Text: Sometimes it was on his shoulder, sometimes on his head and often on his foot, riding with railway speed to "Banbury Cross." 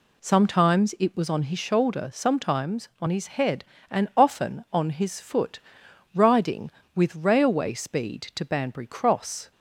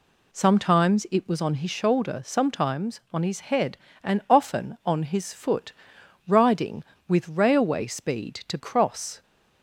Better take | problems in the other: first | skips "Banbury"; at 8.5 s

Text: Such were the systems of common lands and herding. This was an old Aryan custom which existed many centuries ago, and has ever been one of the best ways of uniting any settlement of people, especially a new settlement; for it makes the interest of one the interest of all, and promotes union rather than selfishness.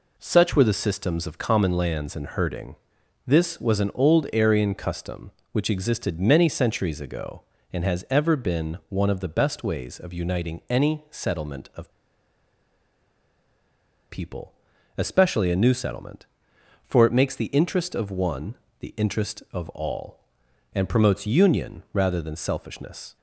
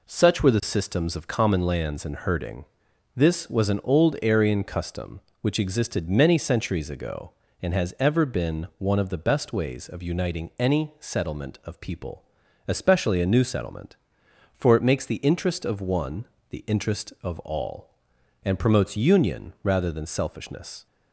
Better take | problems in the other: second | pauses between "of" and "people"; strong; at 11.9 s; 2.1 s long // pauses between "one" and "the"; slight; at 18.5 s; 0.26 s long; slight in the second

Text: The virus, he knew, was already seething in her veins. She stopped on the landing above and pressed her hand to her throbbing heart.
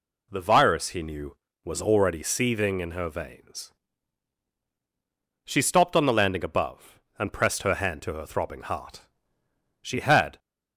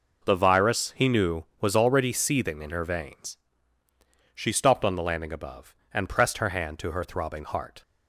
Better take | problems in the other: second | goes on to say "She had"; from 9.8 s on; 0.56 s long

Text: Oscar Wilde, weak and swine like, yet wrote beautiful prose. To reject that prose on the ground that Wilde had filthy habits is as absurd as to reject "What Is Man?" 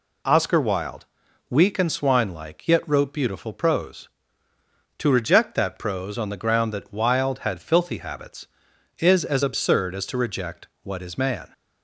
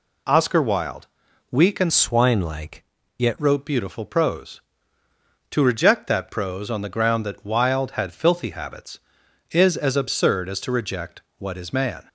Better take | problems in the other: first | changes voice from "swine" to "yet"; from 1.9 to 3.3 s; 1.4 s long // pauses between "reject" and "What"; slight; at 11.1 s; 0.18 s long; slight in the first

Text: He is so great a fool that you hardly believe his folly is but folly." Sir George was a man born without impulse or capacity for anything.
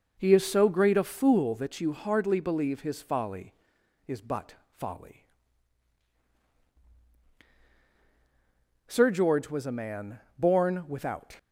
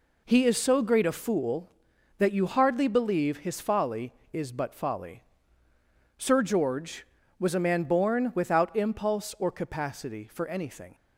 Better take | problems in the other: second | pauses between "man" and "born"; slight; at 10.1 s; 0.18 s long // stops before "impulse or capacity for anything"; at 11.3 s

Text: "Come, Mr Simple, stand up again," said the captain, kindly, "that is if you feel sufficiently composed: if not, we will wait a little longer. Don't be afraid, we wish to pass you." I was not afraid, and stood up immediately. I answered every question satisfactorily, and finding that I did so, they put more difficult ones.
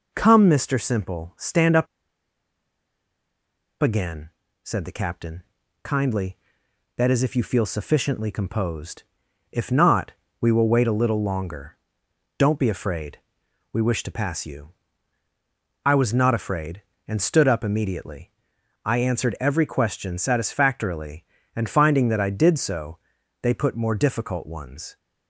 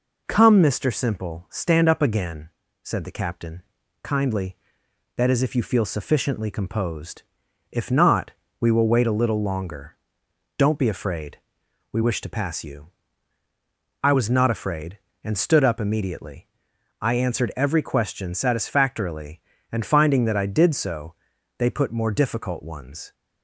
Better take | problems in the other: second | pauses between "up" and "again"; strong; at 1.8 s; 1.9 s long

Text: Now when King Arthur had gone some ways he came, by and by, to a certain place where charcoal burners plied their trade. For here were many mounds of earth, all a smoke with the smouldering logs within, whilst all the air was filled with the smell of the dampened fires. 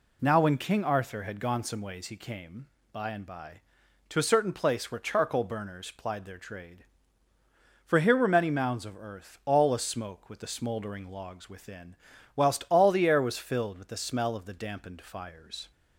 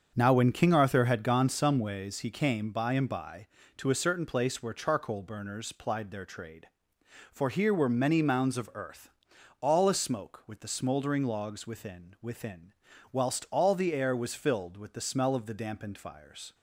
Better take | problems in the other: first | starts louder than the rest; strong; until 1.1 s; 7 dB // says "within" twice; at 12.2 s

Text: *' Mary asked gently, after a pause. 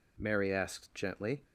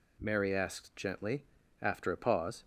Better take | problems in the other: second | stops before "after a pause"; at 1.4 s

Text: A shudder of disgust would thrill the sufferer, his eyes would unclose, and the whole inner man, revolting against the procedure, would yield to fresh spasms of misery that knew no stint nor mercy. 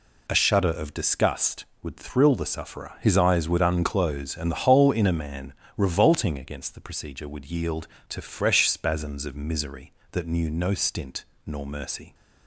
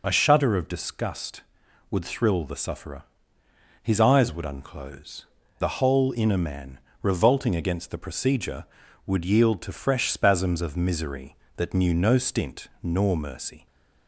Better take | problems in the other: first | skips "and"; at 5.4 s // pauses between "stint" and "nor"; slight; at 12.6 s; 0.16 s long; slight in the first

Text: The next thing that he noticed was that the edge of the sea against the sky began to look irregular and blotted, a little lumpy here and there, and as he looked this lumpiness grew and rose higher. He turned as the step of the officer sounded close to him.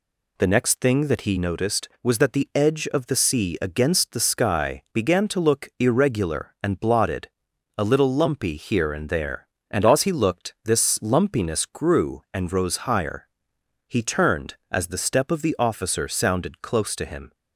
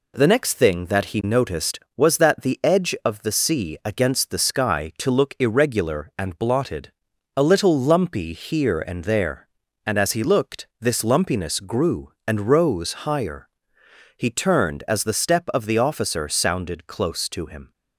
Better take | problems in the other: first | skips "began"; at 4.9 s // pauses between "looked" and "this"; slight; at 10.6 s; 0.16 s long

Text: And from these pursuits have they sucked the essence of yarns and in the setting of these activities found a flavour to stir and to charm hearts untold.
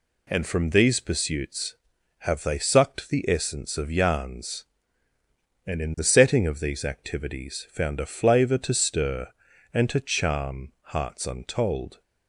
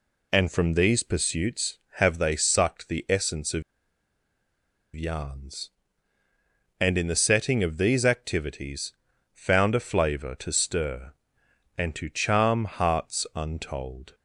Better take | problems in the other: first | pauses between "of" and "yarns"; strong; at 3.6 s; 1.3 s long // pauses between "activities" and "found"; at 8.9 s; 0.40 s long

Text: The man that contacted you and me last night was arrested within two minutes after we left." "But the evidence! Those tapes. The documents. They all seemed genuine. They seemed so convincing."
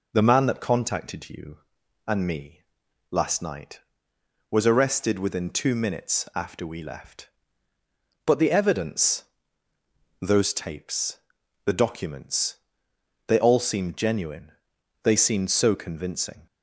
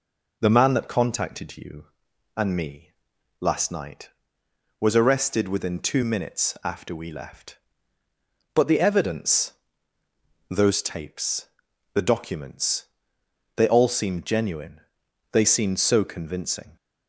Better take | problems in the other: neither | pauses between "me" and "last"; noticeable; the same in both

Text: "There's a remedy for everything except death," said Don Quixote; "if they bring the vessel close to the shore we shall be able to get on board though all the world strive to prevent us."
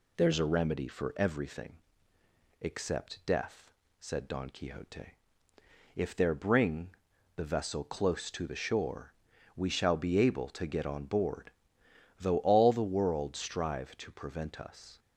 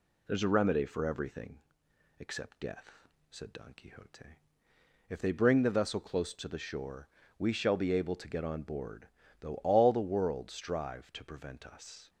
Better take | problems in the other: second | pauses between "everything" and "except"; noticeable; at 1.7 s; 0.84 s long; noticeable in the second // says "there" for "they"; at 6.1 s // pauses between "bring" and "the"; at 6.9 s; 0.40 s long // pauses between "shore" and "we"; at 9.1 s; 0.42 s long; slight in the second // pauses between "board" and "though"; noticeable; at 11.5 s; 0.70 s long; slight in the second

